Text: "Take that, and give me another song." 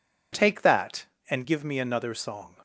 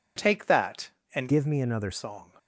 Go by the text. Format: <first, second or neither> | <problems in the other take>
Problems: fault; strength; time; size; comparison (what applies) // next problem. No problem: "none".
first | changes voice from "give" to "another"; from 1.2 to 1.9 s; 0.7 s long